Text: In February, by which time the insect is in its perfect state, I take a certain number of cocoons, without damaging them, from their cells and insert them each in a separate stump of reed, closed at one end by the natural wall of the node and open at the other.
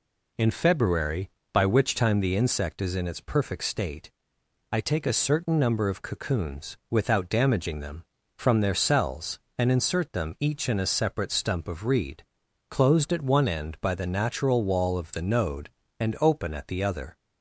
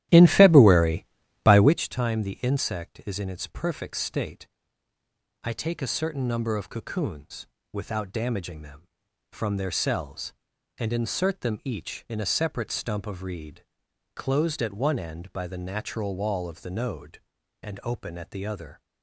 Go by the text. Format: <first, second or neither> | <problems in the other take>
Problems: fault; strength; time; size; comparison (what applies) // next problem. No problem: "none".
first | starts louder than the rest; strong; until 1.8 s; 13.5 dB